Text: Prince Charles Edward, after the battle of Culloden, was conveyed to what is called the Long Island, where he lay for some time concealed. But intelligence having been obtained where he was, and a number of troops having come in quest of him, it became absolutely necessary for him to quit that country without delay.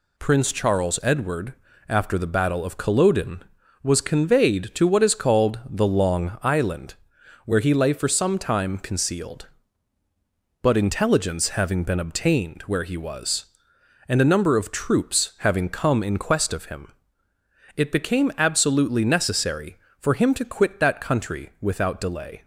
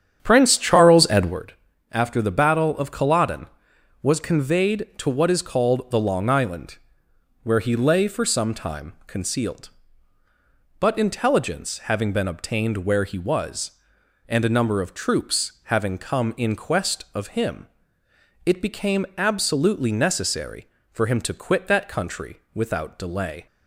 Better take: first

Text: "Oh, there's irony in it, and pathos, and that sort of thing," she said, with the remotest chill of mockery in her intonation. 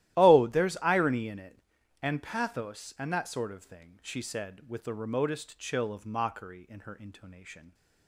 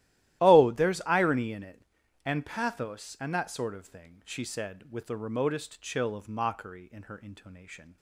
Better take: neither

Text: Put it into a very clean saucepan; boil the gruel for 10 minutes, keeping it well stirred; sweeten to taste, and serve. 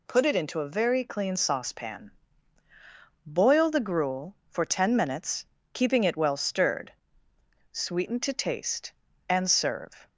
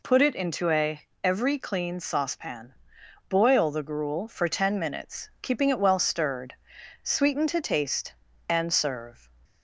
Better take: first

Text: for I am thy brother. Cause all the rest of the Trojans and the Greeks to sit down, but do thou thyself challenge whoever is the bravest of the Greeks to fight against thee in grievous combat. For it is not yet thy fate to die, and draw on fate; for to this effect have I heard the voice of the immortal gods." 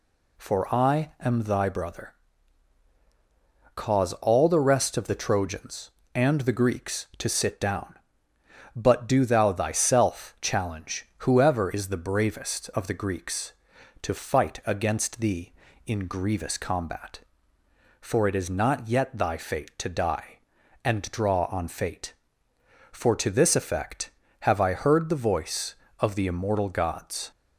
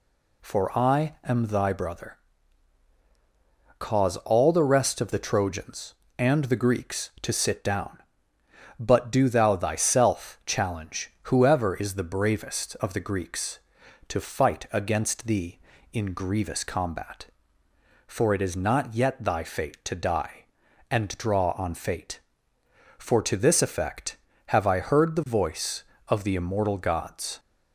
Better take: neither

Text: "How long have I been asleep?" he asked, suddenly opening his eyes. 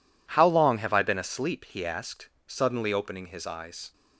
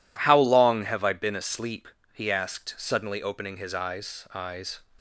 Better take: first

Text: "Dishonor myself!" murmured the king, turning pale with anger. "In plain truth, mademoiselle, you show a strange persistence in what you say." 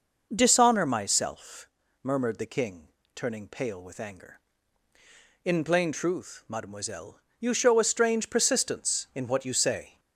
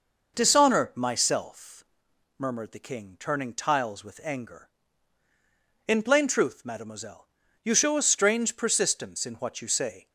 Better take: first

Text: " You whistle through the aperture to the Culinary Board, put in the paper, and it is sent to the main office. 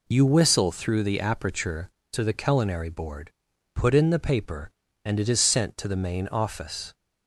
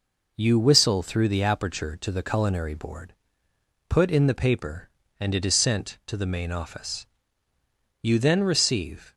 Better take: first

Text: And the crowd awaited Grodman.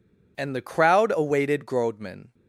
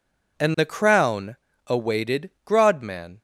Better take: first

